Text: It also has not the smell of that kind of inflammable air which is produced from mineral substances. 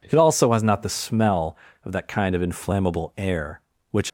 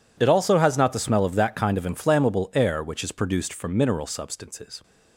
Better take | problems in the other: second | stops before "is produced from mineral substances"; at 4.0 s

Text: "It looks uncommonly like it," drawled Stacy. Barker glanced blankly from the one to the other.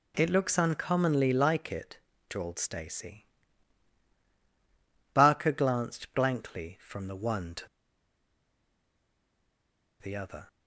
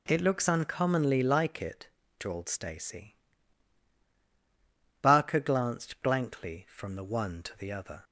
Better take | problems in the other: second | pauses between "to" and "the"; strong; at 7.6 s; 2.3 s long

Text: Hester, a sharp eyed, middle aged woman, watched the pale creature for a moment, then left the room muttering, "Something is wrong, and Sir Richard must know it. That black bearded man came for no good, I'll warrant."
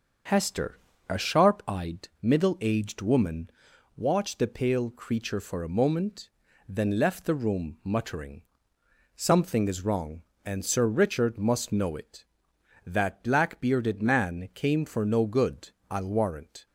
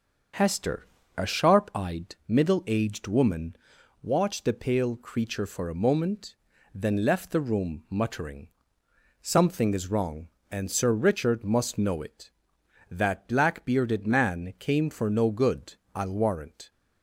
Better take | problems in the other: neither | starts louder than the rest; the same in both

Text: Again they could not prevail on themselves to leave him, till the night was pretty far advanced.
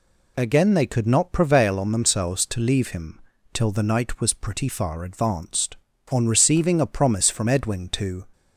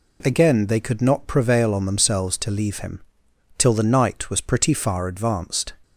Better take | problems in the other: second | goes on to say "On receiving a promise from Edwin to"; strong; from 6.0 s on; 2.2 s long

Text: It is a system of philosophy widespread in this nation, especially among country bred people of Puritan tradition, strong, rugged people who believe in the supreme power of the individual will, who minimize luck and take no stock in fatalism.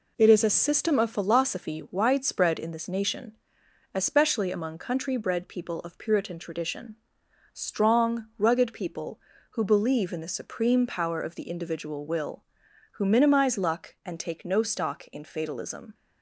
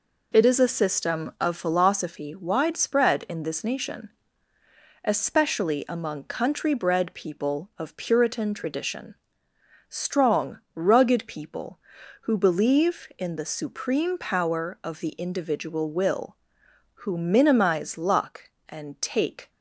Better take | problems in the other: first | stops before "no stock in fatalism"; at 19.4 s

